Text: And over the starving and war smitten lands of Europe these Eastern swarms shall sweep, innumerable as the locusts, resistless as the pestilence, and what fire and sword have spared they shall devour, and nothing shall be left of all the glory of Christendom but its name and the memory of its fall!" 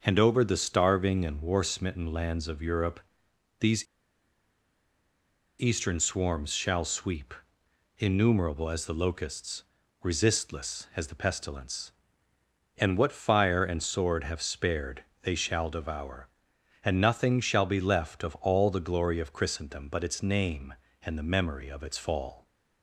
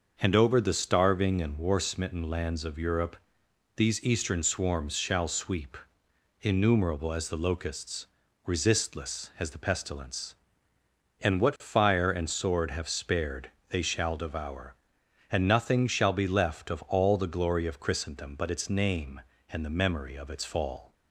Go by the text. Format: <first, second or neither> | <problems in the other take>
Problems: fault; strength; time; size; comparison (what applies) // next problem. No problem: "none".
second | starts louder than the rest; noticeable; until 1.0 s; 6 dB; noticeable in the second // pauses between "Europe" and "these"; noticeable; at 3.0 s; 0.60 s long; noticeable in the second // pauses between "these" and "Eastern"; strong; at 3.8 s; 1.7 s long // pauses between "spared" and "they"; slight; at 15.0 s; 0.18 s long; slight in the second